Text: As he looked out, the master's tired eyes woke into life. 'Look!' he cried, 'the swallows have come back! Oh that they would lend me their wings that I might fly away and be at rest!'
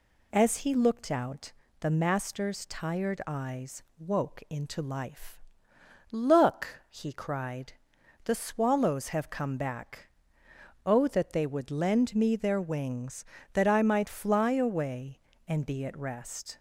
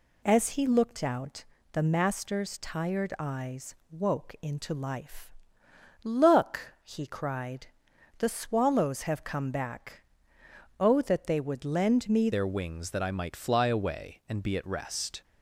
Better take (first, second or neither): first